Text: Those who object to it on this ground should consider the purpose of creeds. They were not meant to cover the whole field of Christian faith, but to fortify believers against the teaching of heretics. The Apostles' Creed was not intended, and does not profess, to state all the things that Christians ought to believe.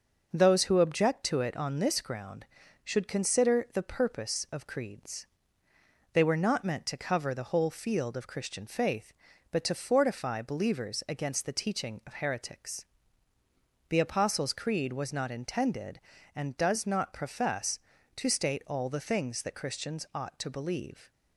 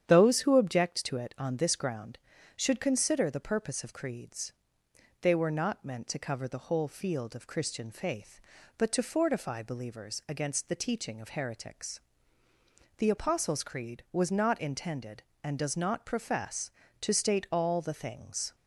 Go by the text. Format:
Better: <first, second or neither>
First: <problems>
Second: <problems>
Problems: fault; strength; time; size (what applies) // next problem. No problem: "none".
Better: first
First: none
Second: starts louder than the rest; strong; until 1.1 s; 9 dB // stops before "that Christians ought to believe"; at 18.5 s